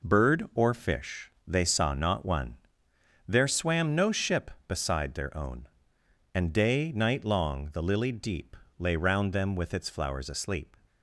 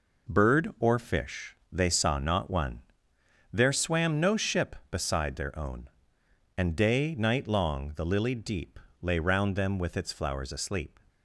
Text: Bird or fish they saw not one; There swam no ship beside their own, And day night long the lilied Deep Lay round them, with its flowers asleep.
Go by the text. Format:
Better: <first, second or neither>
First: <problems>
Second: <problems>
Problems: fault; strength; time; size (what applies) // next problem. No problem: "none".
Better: neither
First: pauses between "fish" and "they"; slight; at 1.3 s; 0.16 s long // pauses between "Deep" and "Lay"; slight; at 8.5 s; 0.22 s long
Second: pauses between "fish" and "they"; slight; at 1.5 s; 0.16 s long // pauses between "Deep" and "Lay"; slight; at 8.7 s; 0.22 s long